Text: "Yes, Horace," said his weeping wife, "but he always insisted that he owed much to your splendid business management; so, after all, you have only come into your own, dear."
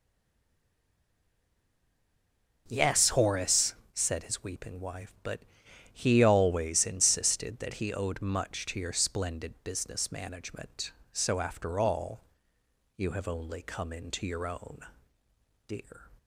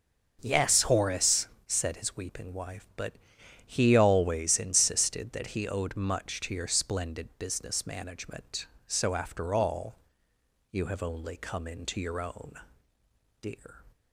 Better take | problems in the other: second | stays silent before the first word; strong; until 2.6 s; 2.6 s long // starts louder than the rest; until 3.6 s; 6.5 dB; also in the second // pauses between "but" and "he"; noticeable; at 5.4 s; 0.50 s long; noticeable in the second

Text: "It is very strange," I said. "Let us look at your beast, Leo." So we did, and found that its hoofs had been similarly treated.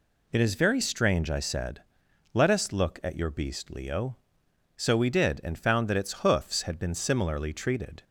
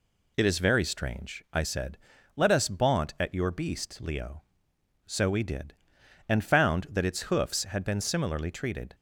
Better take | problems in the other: first | says "baunt" for "look"; at 2.6 s

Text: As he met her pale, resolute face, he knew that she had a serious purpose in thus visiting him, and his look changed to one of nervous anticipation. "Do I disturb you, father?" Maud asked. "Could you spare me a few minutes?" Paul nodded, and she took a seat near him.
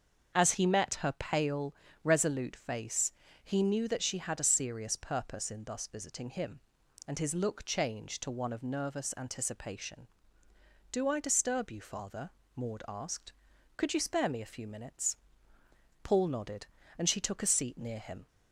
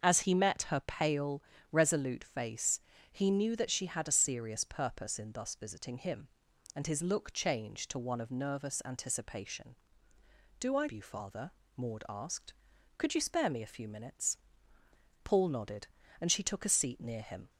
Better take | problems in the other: first | starts louder than the rest; until 1.0 s; 6.5 dB; also in the first // skips "disturb"; at 10.8 s

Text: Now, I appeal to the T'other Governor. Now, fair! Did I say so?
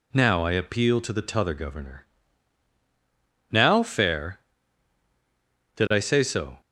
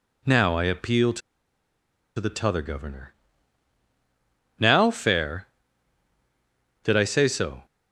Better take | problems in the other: first | pauses between "to" and "the"; at 1.2 s; 0.98 s long

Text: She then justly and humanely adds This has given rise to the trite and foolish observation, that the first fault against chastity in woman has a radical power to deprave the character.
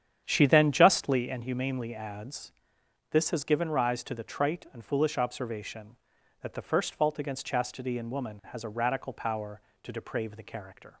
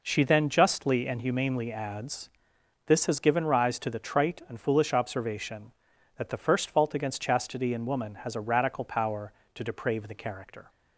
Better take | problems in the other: second | starts louder than the rest; strong; until 1.2 s; 9 dB // pauses between "adds" and "This"; noticeable; at 2.5 s; 0.58 s long; noticeable in the second

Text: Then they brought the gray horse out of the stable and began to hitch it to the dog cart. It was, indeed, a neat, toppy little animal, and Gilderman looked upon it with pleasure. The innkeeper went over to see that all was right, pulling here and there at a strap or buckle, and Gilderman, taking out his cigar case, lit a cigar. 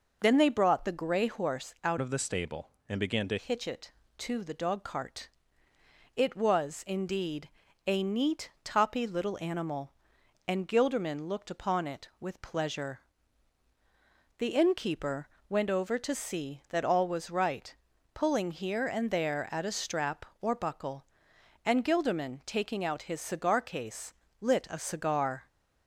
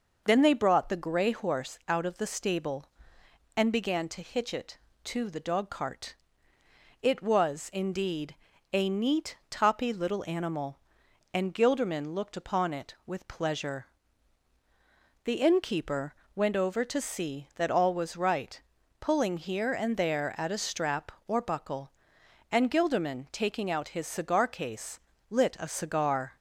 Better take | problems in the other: second | changes voice from "of" to "to"; from 2.0 to 3.3 s; 1.3 s long // pauses between "innkeeper" and "went"; slight; at 15.2 s; 0.22 s long; slight in the second

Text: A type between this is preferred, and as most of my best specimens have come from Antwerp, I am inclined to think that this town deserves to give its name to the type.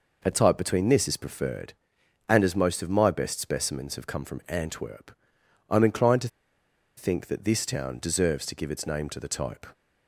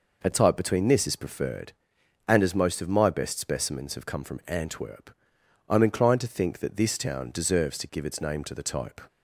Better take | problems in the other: second | pauses between "to" and "think"; noticeable; at 6.2 s; 0.68 s long

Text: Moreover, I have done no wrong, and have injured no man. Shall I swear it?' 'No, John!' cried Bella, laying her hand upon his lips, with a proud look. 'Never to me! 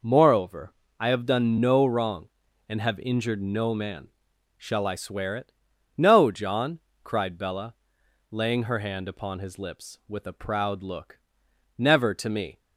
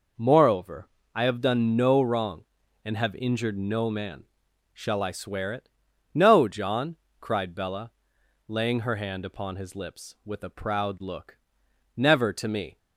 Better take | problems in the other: neither | none

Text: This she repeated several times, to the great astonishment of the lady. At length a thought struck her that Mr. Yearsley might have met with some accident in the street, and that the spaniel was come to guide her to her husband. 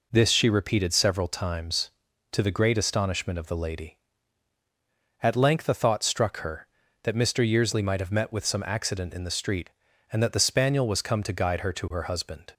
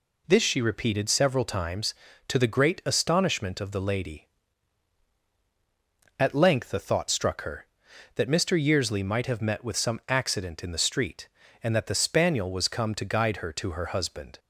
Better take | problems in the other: neither | none

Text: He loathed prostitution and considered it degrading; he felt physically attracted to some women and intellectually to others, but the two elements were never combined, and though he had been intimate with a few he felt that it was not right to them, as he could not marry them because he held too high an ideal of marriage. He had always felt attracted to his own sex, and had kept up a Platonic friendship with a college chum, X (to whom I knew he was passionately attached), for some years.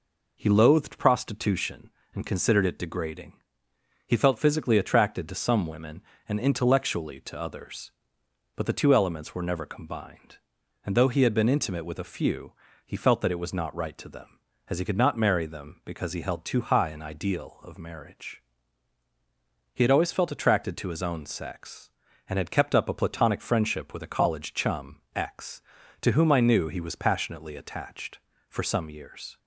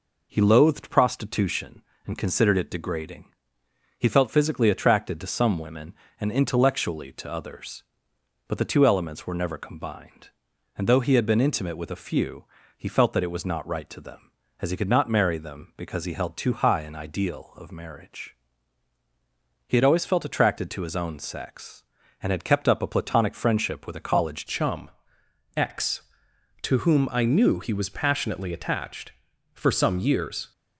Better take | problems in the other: first | pauses between "few" and "he"; slight; at 12.4 s; 0.34 s long; slight in the first // changes voice at "chum"; from 24.4 s on; 6.1 s long

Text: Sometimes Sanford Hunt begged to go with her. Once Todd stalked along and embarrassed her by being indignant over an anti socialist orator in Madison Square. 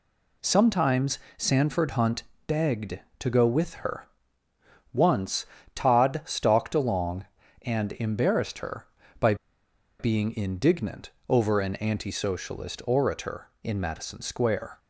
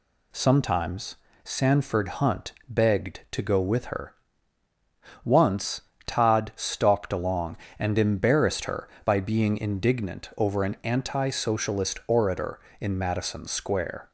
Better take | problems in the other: second | pauses between "Sometimes" and "Sanford"; slight; at 1.1 s; 0.18 s long; slight in the second // pauses between "Hunt" and "begged"; slight; at 2.2 s; 0.24 s long; slight in the second // pauses between "Once" and "Todd"; slight; at 5.4 s; 0.30 s long; slight in the second // pauses between "by" and "being"; noticeable; at 9.3 s; 0.64 s long // pauses between "indignant" and "over"; slight; at 11.1 s; 0.18 s long

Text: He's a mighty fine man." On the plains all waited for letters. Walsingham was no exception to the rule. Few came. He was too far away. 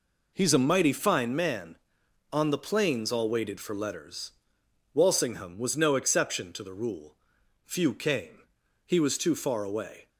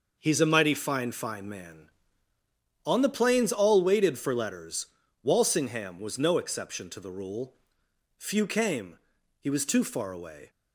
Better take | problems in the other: first | says "fine" twice; at 1.1 s

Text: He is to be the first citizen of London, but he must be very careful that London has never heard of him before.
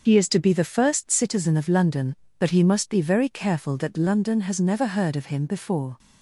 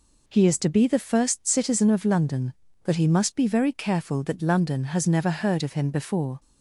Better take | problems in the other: second | loses the start of "He"; at 0.0 s; 50 ms // starts louder than the rest; until 1.0 s; 6.5 dB

